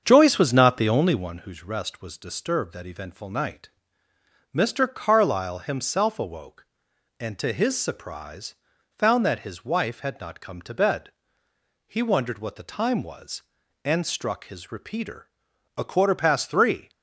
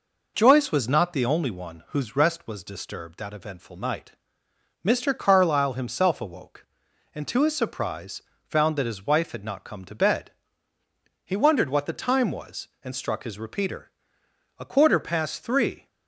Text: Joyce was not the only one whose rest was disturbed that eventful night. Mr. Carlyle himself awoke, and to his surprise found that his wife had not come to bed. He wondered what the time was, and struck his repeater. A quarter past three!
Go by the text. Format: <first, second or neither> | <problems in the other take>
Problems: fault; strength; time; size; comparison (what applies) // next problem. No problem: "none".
second | starts louder than the rest; strong; until 1.5 s; 7 dB // pauses between "surprise" and "found"; at 8.5 s; 0.44 s long; slight in the second